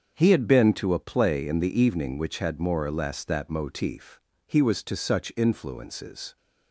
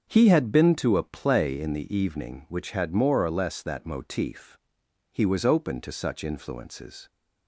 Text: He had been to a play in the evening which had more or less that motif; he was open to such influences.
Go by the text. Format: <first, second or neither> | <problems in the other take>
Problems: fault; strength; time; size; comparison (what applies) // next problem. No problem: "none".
second | starts louder than the rest; until 1.1 s; 7 dB; also in the second // skips "open"; at 4.8 s